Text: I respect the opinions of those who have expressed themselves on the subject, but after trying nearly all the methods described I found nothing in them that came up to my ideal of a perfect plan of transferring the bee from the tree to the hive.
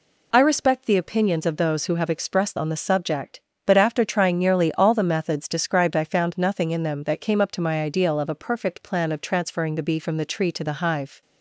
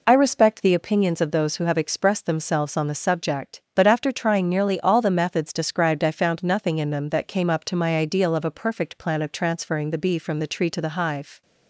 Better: second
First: skips "themselves"; at 2.5 s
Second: none

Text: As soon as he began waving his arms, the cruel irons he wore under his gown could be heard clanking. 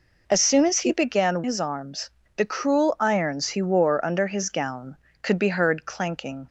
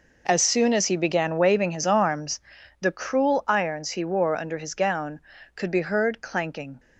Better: second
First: skips "waving"; at 1.4 s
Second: none

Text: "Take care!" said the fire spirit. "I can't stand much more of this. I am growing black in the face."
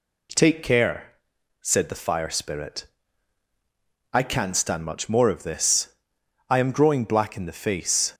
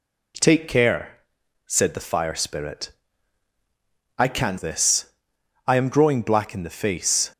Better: first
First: none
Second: skips "stand much more of"; at 4.5 s

